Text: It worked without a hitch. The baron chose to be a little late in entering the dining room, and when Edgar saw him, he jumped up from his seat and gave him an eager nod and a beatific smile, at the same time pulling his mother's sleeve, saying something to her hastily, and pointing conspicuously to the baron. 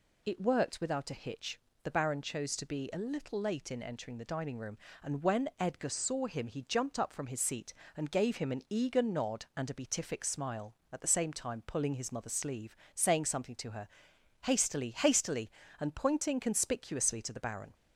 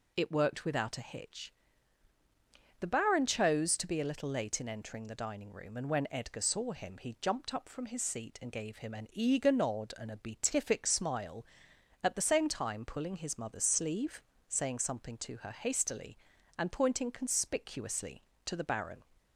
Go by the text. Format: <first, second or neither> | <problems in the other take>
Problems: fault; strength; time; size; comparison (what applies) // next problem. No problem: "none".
second | pauses between "her" and "hastily"; noticeable; at 13.8 s; 0.56 s long // says "hastily" twice; at 14.9 s